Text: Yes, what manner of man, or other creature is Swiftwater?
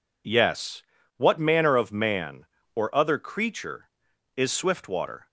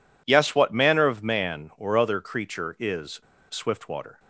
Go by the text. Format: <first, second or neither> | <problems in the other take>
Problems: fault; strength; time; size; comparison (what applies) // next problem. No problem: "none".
first | pauses between "is" and "Swiftwater"; slight; at 3.1 s; 0.31 s long